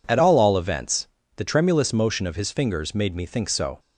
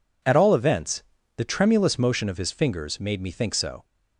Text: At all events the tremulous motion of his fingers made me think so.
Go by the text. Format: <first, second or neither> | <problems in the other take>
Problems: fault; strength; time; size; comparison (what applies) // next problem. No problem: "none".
second | says "all" twice; at 0.3 s // pauses between "events" and "the"; slight; at 1.0 s; 0.30 s long; slight in the second